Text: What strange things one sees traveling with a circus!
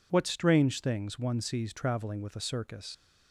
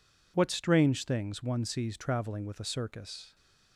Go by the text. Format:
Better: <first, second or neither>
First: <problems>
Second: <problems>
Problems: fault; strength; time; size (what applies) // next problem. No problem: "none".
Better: second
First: leaves "circus" unfinished; at 2.9 s; 160 ms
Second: none